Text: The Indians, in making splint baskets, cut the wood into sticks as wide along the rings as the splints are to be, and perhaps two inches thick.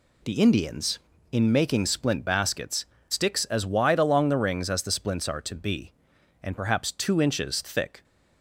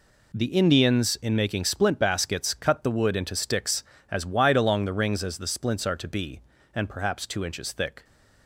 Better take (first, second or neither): second